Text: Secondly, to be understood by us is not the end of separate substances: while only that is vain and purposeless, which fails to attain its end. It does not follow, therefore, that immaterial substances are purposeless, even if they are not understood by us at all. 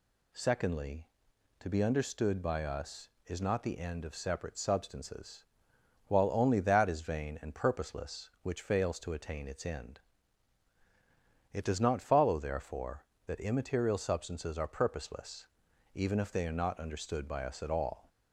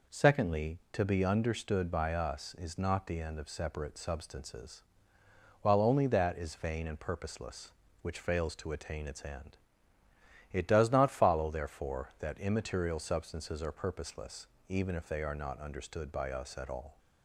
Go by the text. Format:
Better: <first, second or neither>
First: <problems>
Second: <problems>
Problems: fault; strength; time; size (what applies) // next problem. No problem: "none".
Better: neither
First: none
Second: none